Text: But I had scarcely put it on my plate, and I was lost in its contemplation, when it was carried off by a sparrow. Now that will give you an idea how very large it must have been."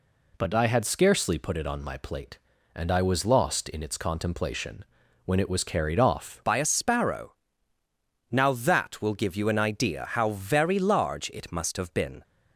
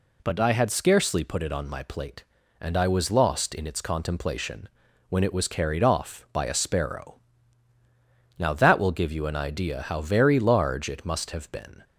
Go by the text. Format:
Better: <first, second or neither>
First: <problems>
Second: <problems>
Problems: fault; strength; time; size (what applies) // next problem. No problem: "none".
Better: second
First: changes voice at "by"; from 6.4 s on; 5.8 s long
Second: none